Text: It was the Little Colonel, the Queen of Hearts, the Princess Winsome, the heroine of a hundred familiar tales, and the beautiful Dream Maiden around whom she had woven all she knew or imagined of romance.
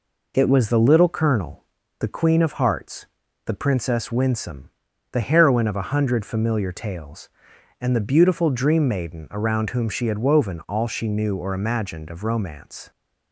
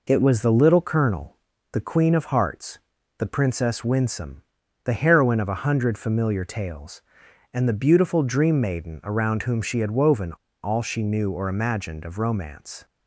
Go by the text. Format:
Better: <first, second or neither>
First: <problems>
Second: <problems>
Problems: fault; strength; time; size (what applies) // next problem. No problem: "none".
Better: first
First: none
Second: pauses between "woven" and "all"; slight; at 10.3 s; 0.31 s long